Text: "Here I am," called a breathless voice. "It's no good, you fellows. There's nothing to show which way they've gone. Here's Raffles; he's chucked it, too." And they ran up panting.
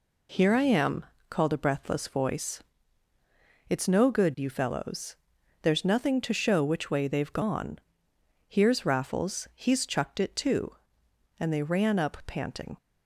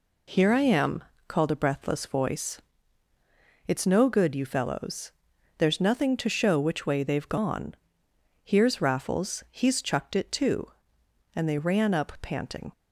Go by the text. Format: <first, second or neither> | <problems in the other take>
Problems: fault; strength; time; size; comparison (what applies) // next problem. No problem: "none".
neither | none